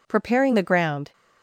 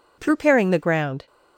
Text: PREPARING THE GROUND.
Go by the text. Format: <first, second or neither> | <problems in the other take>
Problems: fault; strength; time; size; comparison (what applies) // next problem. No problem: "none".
neither | none